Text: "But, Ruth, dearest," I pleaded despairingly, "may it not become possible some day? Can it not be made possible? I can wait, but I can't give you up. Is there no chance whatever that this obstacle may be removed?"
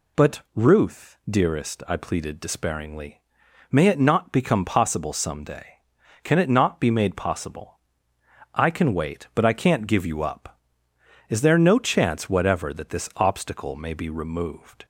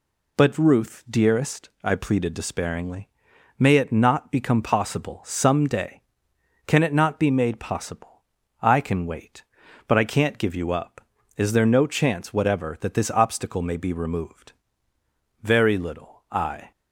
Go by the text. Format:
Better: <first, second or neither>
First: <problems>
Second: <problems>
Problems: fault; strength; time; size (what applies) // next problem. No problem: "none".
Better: first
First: none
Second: goes on to say "Very little I"; noticeable; from 15.4 s on; 1.2 s long